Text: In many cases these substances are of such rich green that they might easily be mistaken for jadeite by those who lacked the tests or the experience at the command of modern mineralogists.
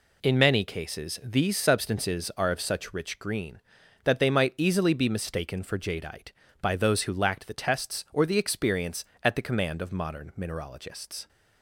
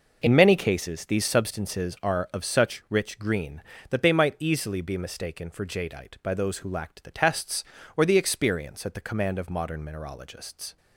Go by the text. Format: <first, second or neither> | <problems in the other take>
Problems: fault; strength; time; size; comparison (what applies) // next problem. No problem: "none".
neither | none